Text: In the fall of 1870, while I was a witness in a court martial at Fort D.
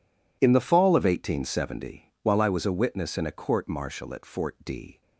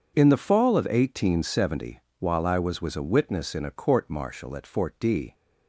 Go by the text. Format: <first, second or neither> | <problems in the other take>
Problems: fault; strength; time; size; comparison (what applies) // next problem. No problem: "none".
first | says "was" twice; at 2.7 s